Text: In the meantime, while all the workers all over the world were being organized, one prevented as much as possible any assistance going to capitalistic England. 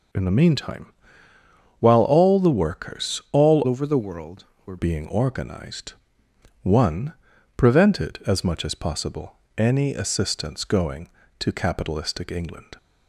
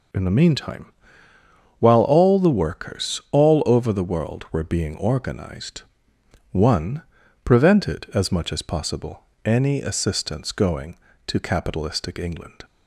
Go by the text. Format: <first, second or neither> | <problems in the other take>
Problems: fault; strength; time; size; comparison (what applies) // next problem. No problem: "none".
second | changes voice from "over" to "were"; from 3.6 to 4.7 s; 1.1 s long // pauses between "one" and "prevented"; at 7.1 s; 0.44 s long; also in the second // pauses between "possible" and "any"; slight; at 9.3 s; 0.20 s long; slight in the second